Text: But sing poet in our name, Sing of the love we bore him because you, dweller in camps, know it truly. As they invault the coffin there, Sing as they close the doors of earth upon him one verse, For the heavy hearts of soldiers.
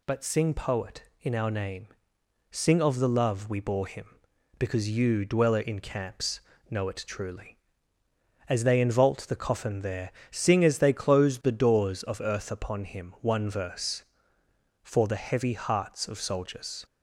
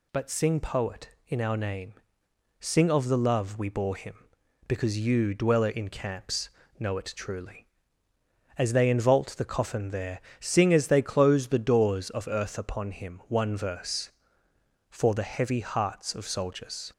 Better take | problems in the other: neither | none

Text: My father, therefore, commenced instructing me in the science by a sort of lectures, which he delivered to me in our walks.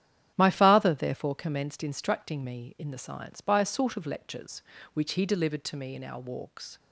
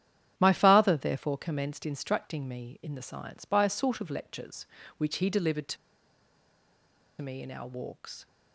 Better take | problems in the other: first | starts louder than the rest; strong; until 1.3 s; 10 dB; strong in the first // pauses between "to" and "me"; strong; at 5.7 s; 1.4 s long

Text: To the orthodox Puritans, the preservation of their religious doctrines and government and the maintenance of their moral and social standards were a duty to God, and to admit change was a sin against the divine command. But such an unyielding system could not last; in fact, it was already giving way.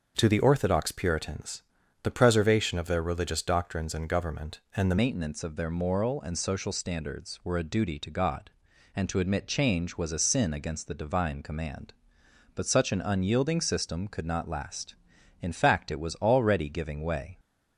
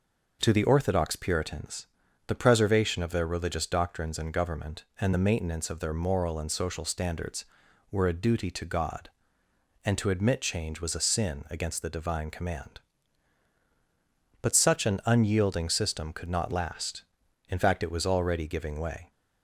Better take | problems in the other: second | starts louder than the rest; until 1.1 s; 6.5 dB // changes voice at "maintenance"; from 4.9 s on; 12.4 s long

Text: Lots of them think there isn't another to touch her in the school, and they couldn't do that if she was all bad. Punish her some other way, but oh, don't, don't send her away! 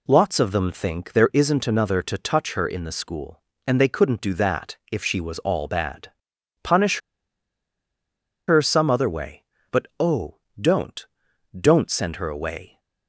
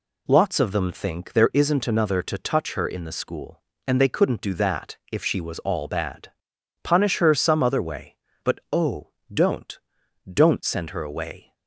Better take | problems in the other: second | pauses between "that" and "if"; slight; at 4.7 s; 0.16 s long; slight in the second // pauses between "Punish" and "her"; strong; at 6.9 s; 1.5 s long

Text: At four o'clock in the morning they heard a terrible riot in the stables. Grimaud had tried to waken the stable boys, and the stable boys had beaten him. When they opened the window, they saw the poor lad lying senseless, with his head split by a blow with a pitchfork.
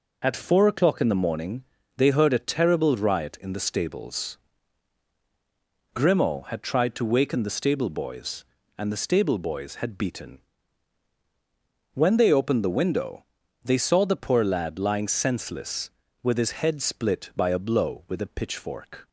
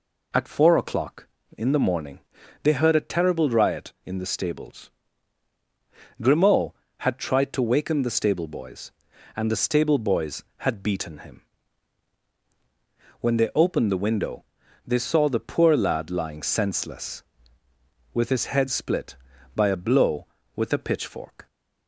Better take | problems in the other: second | pauses between "morning" and "they"; slight; at 1.6 s; 0.32 s long; also in the second // skips "him"; at 11.1 s

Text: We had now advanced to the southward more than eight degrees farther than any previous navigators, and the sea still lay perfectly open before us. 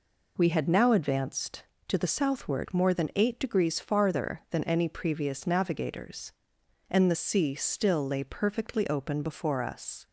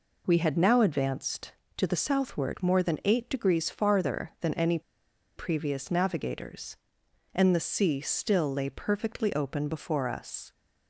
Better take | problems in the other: first | pauses between "any" and "previous"; noticeable; at 4.7 s; 0.57 s long

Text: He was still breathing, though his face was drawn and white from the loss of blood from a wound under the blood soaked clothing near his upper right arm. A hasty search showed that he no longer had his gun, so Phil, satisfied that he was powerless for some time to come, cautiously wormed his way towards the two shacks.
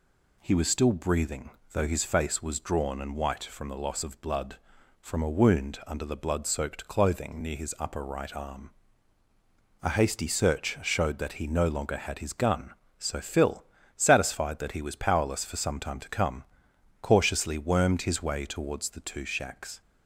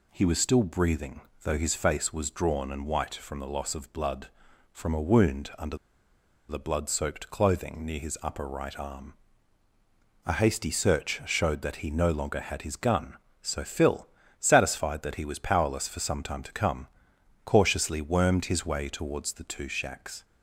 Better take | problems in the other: first | pauses between "under" and "the"; noticeable; at 5.7 s; 0.73 s long

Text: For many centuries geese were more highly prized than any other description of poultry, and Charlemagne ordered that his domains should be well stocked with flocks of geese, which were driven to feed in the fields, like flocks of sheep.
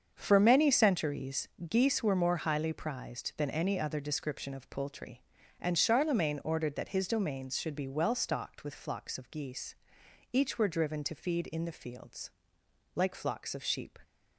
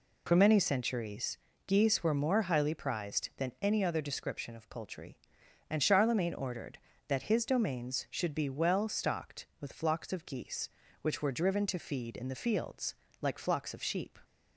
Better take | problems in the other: second | starts louder than the rest; until 1.1 s; 7 dB // pauses between "centuries" and "geese"; slight; at 1.4 s; 0.22 s long; slight in the second // says "each" for "which"; at 10.3 s

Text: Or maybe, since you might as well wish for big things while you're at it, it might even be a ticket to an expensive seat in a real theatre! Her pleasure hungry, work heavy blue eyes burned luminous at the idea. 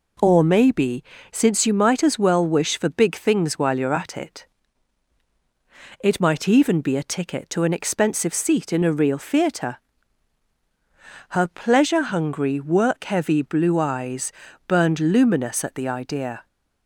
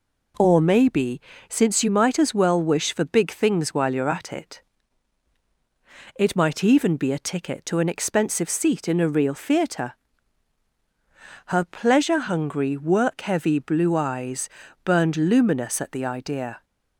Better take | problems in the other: neither | pauses between "eyes" and "burned"; slight; the same in both

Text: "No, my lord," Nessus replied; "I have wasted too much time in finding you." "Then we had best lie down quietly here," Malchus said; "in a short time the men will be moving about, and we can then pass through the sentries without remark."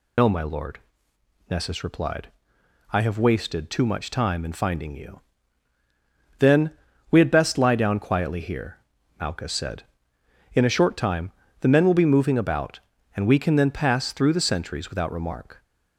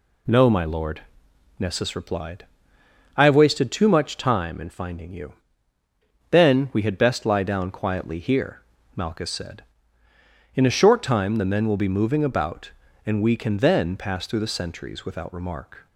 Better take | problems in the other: second | loses the start of "No"; at 0.1 s; 45 ms // pauses between "Then" and "we"; at 6.7 s; 0.40 s long // pauses between "time" and "the"; slight; at 11.3 s; 0.30 s long

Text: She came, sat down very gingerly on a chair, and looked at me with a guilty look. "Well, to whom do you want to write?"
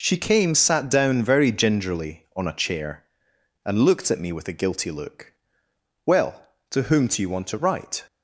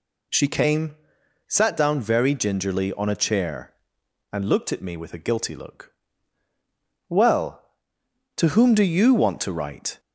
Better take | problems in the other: neither | none

